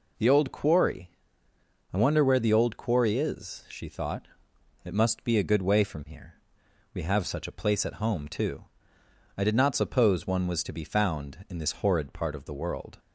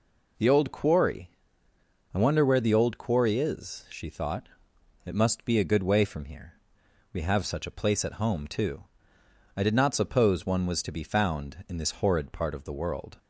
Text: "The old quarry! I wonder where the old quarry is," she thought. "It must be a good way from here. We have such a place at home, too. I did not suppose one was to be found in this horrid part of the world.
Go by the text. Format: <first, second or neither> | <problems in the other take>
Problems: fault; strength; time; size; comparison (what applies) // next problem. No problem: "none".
neither | none